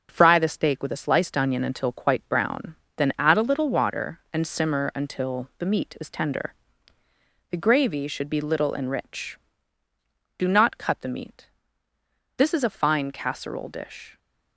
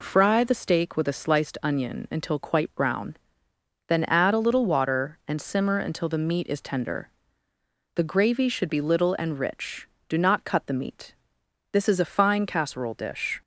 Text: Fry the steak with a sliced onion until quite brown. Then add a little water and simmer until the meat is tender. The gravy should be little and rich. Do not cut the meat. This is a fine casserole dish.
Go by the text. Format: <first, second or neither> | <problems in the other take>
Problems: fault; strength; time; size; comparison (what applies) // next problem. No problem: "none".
second | gets quieter; noticeable; throughout; 5 dB